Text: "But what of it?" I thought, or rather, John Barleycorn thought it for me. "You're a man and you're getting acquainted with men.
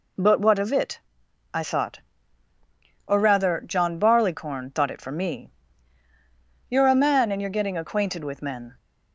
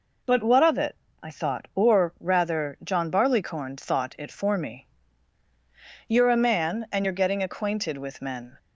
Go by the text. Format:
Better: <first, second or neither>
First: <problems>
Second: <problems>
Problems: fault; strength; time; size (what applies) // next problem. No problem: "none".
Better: neither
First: none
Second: none